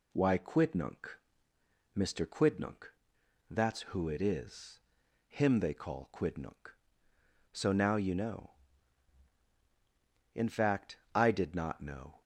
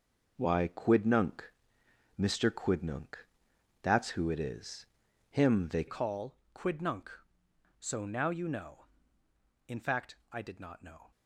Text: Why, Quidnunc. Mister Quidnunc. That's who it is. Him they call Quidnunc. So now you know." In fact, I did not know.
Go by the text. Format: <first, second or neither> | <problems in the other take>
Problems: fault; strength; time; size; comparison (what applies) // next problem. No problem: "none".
first | changes voice at "call"; from 5.8 s on; 5.3 s long // pauses between "call" and "Quidnunc"; slight; at 6.3 s; 0.18 s long